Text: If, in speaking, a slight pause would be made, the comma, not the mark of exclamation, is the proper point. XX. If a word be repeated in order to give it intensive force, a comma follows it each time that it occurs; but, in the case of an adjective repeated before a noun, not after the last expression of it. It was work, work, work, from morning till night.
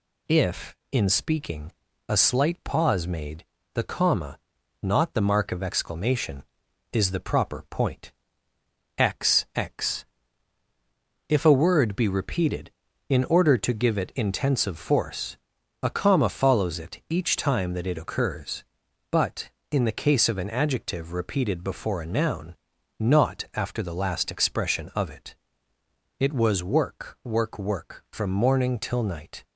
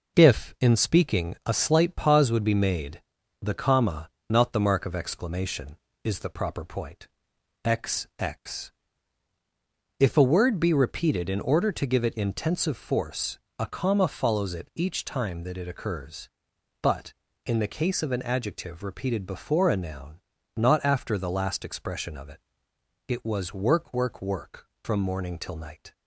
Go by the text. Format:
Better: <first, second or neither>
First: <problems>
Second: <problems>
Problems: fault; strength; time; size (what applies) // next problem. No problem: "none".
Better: second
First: skips "would be"; at 3.0 s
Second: none